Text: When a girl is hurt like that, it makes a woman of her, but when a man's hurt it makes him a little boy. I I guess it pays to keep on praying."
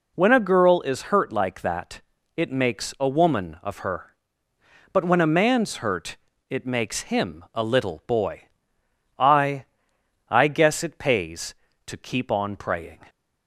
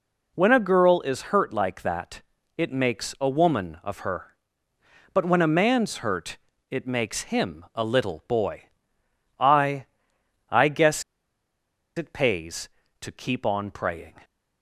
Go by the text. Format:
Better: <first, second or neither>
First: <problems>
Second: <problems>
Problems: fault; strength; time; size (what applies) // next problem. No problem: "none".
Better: first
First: pauses between "hurt" and "it"; slight; at 6.1 s; 0.32 s long // pauses between "I" and "I"; noticeable; at 9.6 s; 0.66 s long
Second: pauses between "hurt" and "it"; slight; at 6.3 s; 0.32 s long // pauses between "I" and "I"; noticeable; at 9.8 s; 0.66 s long // pauses between "guess" and "it"; noticeable; at 11.0 s; 0.94 s long